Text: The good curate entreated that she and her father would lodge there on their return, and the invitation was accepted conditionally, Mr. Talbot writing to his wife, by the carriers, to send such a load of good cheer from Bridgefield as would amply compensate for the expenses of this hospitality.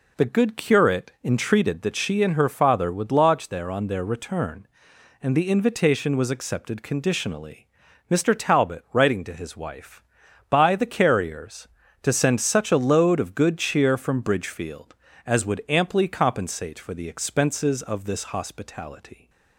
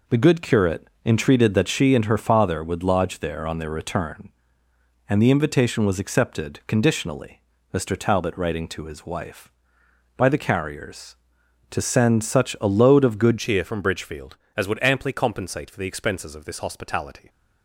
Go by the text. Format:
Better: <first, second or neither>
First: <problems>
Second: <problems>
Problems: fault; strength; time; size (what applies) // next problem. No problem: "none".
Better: first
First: none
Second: pauses between "curate" and "entreated"; slight; at 0.8 s; 0.18 s long // changes voice at "cheer"; from 13.3 s on; 3.9 s long